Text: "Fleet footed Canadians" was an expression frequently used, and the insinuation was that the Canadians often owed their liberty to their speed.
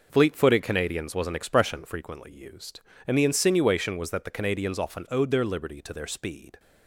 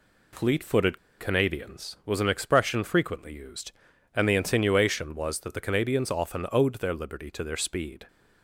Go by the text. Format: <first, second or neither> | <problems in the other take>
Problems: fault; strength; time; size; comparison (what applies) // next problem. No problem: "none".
first | pauses between "footed" and "Canadians"; slight; at 0.9 s; 0.21 s long